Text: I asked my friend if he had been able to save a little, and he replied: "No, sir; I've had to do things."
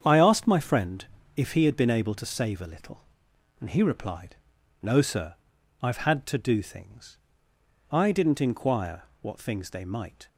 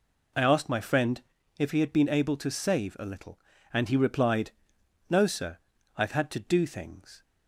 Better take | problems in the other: second | starts louder than the rest; strong; until 1.0 s; 8 dB // pauses between "friend" and "if"; slight; at 1.0 s; 0.30 s long; slight in the second // goes on to say "I didn't inquire what things they might"; strong; from 7.9 s on; 2.3 s long

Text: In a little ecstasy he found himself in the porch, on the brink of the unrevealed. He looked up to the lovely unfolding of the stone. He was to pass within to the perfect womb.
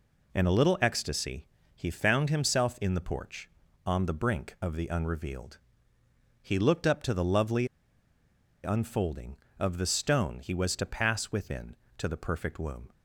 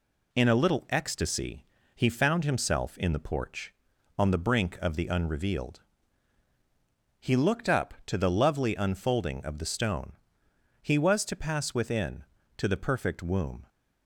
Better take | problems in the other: second | pauses between "ecstasy" and "he"; slight; at 1.4 s; 0.28 s long; slight in the second // pauses between "lovely" and "unfolding"; noticeable; at 7.6 s; 0.97 s long

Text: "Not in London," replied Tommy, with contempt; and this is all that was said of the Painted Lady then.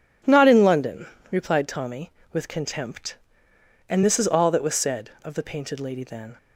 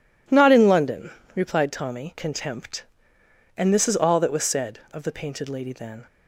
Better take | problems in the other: first | skips "with"; at 2.1 s

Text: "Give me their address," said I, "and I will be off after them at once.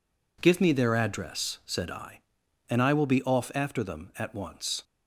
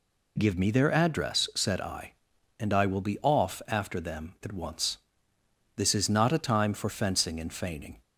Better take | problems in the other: first | goes on to say "This is not a time for fencing and feigning"; strong; from 5.7 s on; 2.2 s long

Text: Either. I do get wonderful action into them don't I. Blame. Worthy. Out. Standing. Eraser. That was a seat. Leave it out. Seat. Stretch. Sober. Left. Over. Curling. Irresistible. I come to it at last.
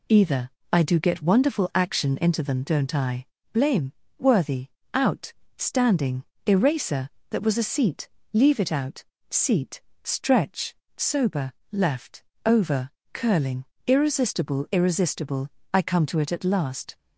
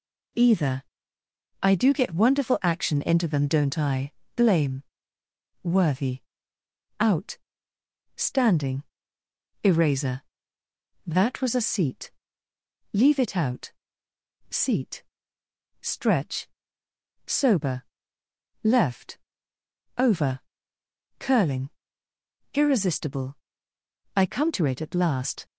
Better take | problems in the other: second | says "Irresistible" twice; at 14.7 s

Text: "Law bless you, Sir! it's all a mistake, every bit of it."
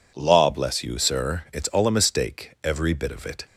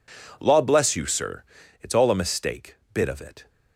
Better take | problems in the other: first | skips "every"; at 2.8 s

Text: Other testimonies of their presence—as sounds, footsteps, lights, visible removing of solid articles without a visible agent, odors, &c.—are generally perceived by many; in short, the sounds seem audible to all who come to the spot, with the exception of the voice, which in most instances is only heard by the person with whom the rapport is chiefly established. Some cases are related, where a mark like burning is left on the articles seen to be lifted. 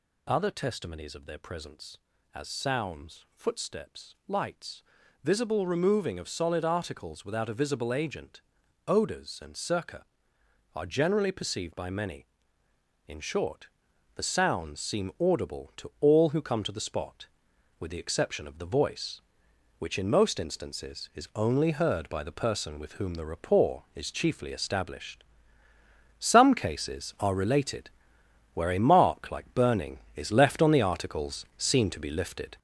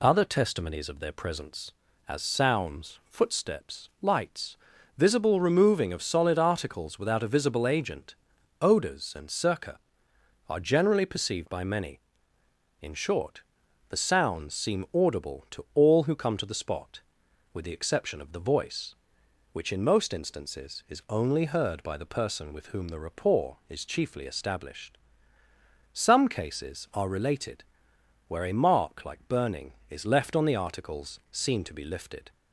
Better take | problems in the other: second | gets louder; noticeable; throughout; 6 dB

